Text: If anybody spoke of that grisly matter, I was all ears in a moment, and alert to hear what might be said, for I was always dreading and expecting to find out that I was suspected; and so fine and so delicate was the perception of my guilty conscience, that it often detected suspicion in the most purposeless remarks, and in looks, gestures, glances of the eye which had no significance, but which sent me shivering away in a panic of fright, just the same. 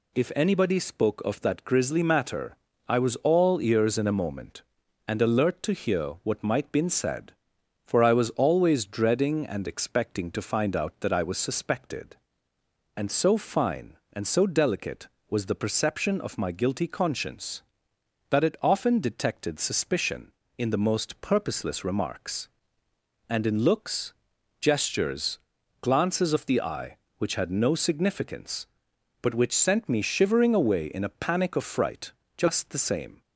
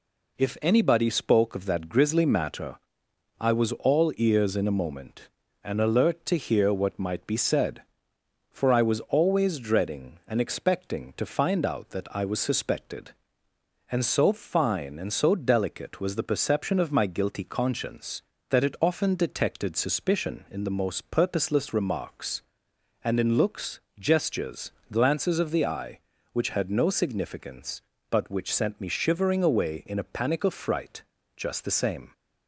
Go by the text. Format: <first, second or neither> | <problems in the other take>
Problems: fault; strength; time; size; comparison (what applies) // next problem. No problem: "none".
second | says "been" for "be"; at 6.7 s